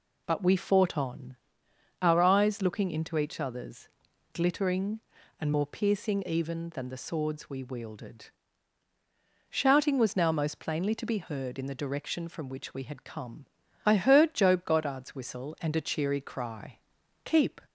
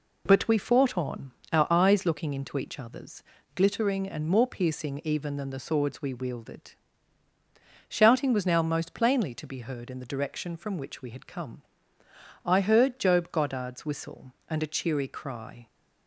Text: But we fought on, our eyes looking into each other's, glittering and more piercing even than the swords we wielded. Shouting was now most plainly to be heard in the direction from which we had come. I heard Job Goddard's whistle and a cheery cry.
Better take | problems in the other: second | goes on to say "Keep"; slight; from 17.2 s on; 0.36 s long

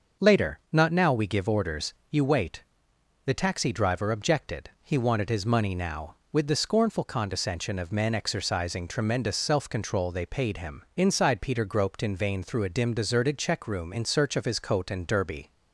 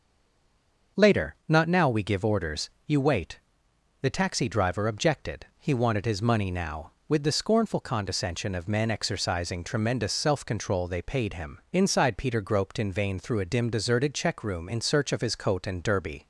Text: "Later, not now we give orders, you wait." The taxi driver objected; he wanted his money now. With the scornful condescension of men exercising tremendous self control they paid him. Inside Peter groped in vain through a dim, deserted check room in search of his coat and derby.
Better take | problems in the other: first | stays silent before the first word; slight; until 0.9 s; 0.9 s long // starts louder than the rest; until 2.1 s; 6.5 dB; also in the first

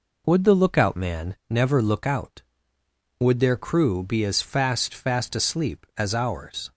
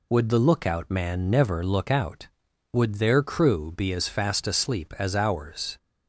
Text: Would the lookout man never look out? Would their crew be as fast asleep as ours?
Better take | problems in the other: second | says "fast" twice; at 4.9 s

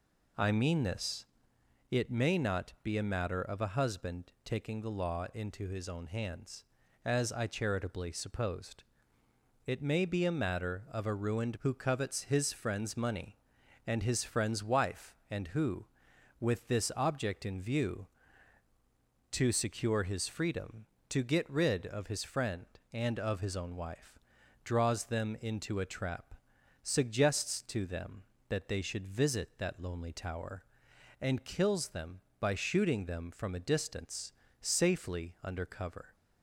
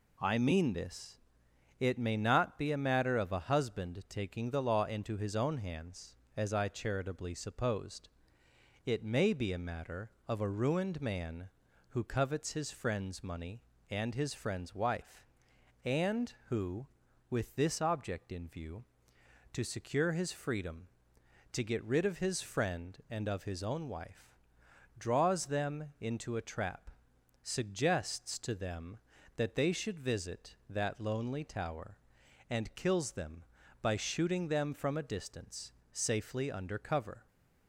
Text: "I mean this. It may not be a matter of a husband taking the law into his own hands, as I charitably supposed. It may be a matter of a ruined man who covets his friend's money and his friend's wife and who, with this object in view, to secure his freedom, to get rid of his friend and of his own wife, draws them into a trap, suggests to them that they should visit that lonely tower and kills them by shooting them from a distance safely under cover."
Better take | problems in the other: second | skips "man"; at 11.5 s // pauses between "distance" and "safely"; slight; at 34.3 s; 0.28 s long; slight in the second

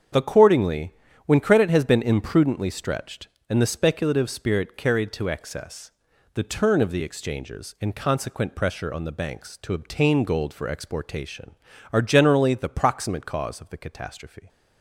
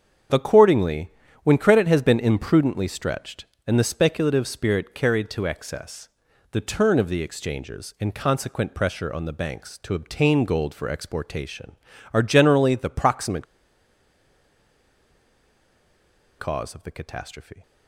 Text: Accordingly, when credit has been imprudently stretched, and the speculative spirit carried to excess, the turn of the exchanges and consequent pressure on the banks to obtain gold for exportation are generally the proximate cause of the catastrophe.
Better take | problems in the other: first | starts louder than the rest; strong; until 1.6 s; 7.5 dB; strong in the first // pauses between "proximate" and "cause"; strong; at 13.4 s; 2.9 s long

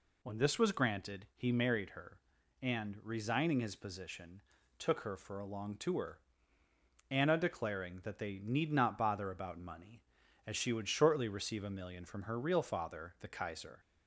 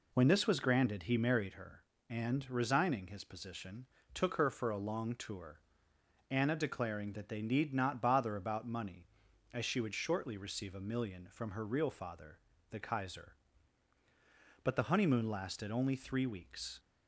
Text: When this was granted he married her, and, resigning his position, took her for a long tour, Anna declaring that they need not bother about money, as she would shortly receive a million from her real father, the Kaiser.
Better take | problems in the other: first | goes on to say "But the honeymoon lasted only three weeks"; strong; from 14.6 s on; 2.1 s long

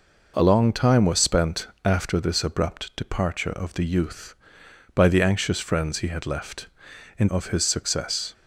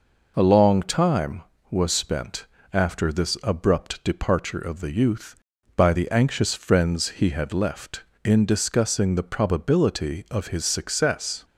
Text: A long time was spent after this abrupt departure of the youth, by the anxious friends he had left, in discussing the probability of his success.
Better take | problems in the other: second | pauses between "spent" and "after"; slight; at 1.6 s; 0.16 s long; slight in the second // skips "discussing the probability"; at 7.2 s

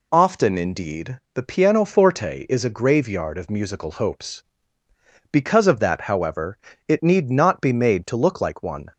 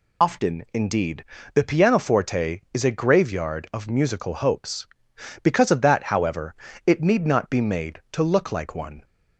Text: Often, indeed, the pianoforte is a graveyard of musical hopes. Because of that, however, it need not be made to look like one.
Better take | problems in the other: first | loses the start of "Often"; at 0.2 s; 80 ms

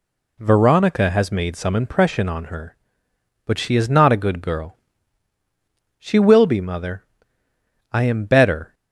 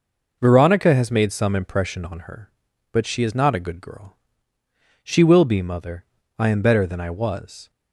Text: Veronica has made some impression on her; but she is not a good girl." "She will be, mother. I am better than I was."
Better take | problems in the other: second | stops before "than I was"; at 8.7 s

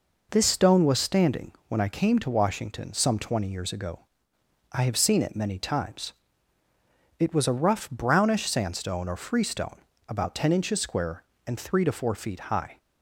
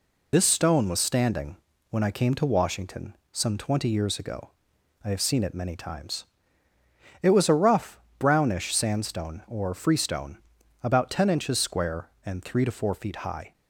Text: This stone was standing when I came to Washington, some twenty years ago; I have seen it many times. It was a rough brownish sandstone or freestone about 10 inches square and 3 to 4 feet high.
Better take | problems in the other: first | loses the start of "This"; at 0.3 s; 55 ms // pauses between "standing" and "when"; slight; at 1.5 s; 0.36 s long; slight in the first // pauses between "rough" and "brownish"; slight; at 7.9 s; 0.18 s long // pauses between "freestone" and "about"; at 10.3 s; 0.44 s long; slight in the first

